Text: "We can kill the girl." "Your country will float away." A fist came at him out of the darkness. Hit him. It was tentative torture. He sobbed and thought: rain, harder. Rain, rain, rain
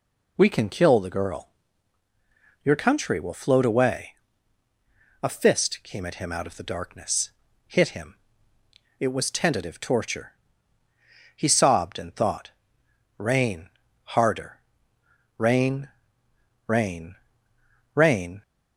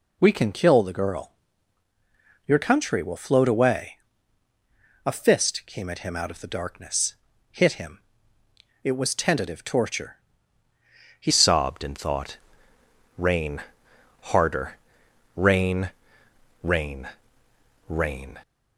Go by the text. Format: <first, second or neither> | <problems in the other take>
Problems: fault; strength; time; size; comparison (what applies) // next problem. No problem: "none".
first | changes voice at "sobbed"; from 11.2 s on; 7.1 s long